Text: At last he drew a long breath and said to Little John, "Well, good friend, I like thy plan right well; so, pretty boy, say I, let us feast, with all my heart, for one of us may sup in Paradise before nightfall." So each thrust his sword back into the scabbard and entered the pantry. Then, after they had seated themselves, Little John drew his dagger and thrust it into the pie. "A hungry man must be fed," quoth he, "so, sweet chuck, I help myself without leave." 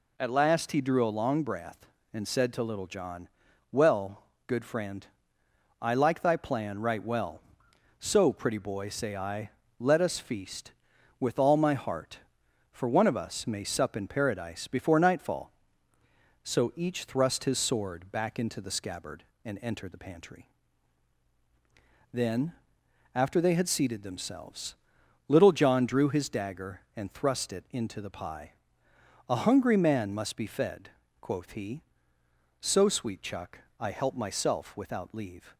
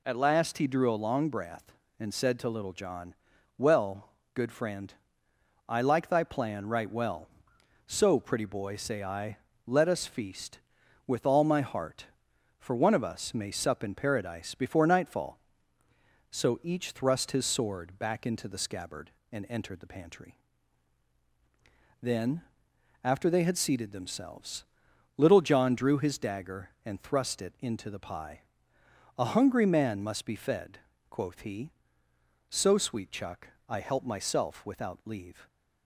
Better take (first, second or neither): neither